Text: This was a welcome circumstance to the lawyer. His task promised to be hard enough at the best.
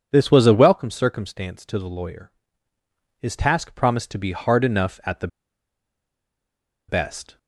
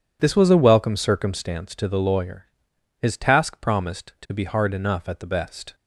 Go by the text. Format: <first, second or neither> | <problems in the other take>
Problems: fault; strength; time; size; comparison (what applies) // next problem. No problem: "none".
second | pauses between "the" and "best"; strong; at 5.2 s; 1.6 s long